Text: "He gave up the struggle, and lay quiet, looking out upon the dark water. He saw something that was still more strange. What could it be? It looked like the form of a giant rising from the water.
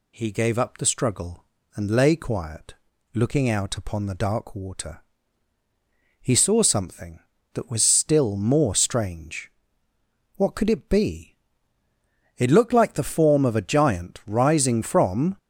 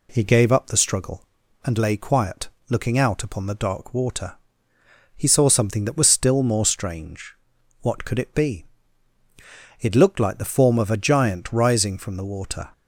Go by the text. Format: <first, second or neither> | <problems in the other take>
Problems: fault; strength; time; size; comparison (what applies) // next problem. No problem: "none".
second | stops before "the water"; at 15.3 s